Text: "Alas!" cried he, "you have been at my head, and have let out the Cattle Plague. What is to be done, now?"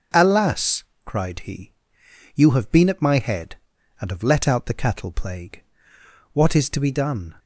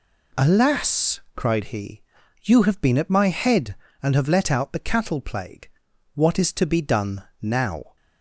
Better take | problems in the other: second | starts louder than the rest; until 1.3 s; 6.5 dB // stops before "now"; at 7.3 s

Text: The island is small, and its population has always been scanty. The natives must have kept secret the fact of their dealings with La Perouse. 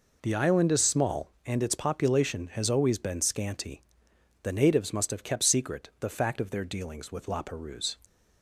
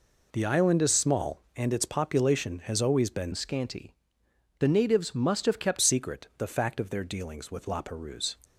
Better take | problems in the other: first | changes voice from "scanty" to "kept"; from 3.3 to 5.7 s; 2.4 s long

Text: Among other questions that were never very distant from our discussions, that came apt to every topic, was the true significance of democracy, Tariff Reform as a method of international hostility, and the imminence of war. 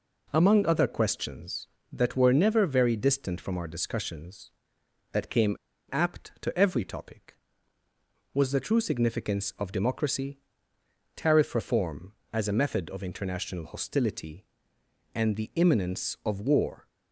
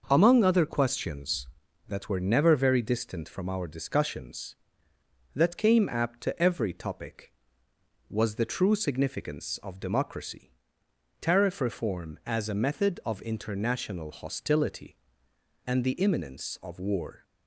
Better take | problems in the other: second | pauses between "came" and "apt"; slight; at 5.5 s; 0.32 s long

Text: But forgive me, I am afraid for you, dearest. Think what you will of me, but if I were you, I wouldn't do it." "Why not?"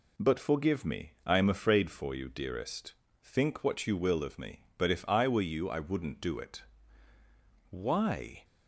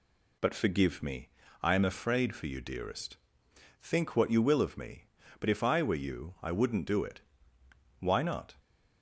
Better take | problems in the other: second | stops before "not"; at 8.4 s

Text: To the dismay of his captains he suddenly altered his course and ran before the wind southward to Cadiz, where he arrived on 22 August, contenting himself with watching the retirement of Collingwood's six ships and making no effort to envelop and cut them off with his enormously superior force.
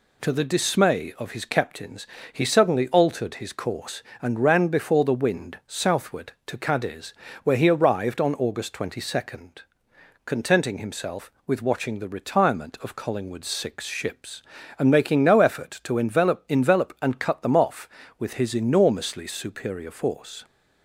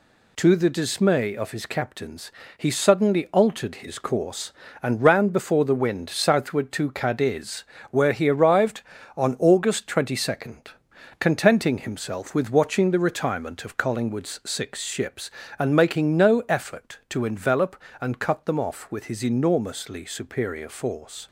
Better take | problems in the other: second | pauses between "captains" and "he"; slight; at 2.0 s; 0.26 s long; slight in the second // says "envelop" twice; at 16.4 s

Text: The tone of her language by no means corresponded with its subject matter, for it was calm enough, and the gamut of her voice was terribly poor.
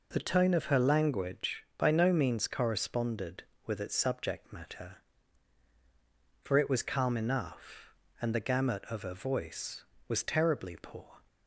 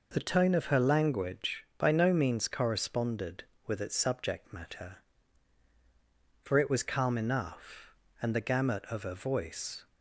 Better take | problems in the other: first | stops before "was terribly poor"; at 9.8 s

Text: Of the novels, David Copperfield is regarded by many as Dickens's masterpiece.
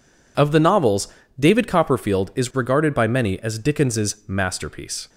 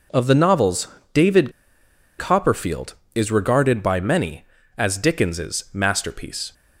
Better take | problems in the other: first | pauses between "David" and "Copperfield"; noticeable; at 1.5 s; 0.67 s long

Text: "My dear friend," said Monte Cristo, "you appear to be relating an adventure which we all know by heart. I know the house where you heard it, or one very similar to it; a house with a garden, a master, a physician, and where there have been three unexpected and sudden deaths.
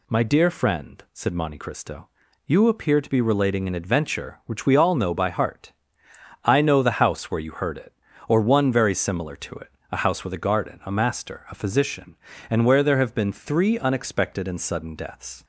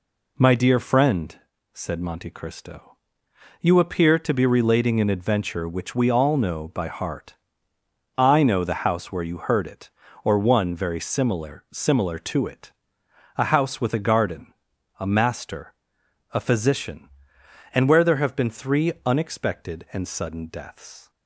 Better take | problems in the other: first | says "similar" twice; at 11.7 s

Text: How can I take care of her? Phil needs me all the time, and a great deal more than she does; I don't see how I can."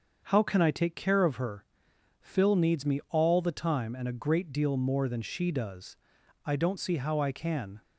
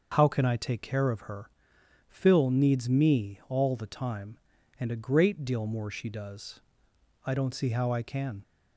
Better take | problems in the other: first | starts louder than the rest; noticeable; until 1.1 s; 6 dB; also in the first // skips "than"; at 5.8 s

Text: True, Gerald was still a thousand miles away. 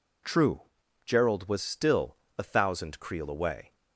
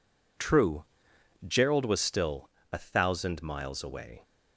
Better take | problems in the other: second | pauses between "still" and "a"; slight; at 2.1 s; 0.22 s long; slight in the second // says "creel" for "miles"; at 2.9 s

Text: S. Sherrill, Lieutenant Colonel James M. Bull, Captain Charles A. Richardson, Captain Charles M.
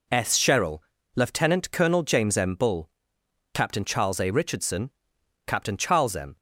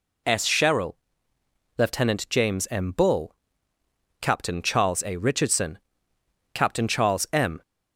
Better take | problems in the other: first | skips "Colonel"; at 2.2 s

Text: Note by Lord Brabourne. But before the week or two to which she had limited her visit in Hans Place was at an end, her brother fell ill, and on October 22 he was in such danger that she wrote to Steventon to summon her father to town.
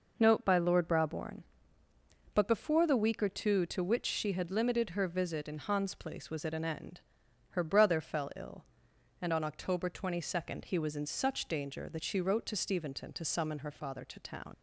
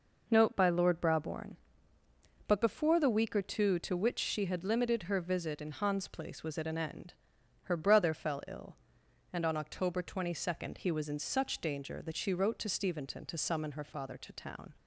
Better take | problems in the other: second | leaves "town" unfinished; at 14.5 s; 105 ms

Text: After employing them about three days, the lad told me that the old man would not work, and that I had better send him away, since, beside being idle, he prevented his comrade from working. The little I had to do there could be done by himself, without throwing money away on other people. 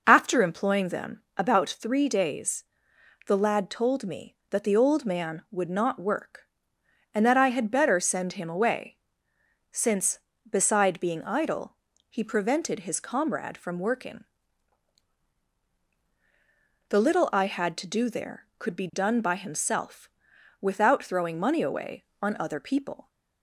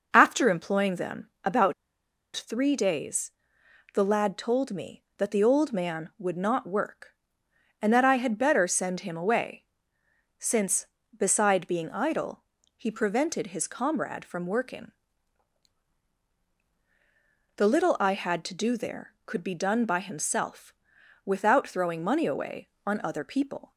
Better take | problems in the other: first | pauses between "them" and "about"; slight; at 1.2 s; 0.16 s long; slight in the first // pauses between "about" and "three"; noticeable; at 1.7 s; 0.63 s long

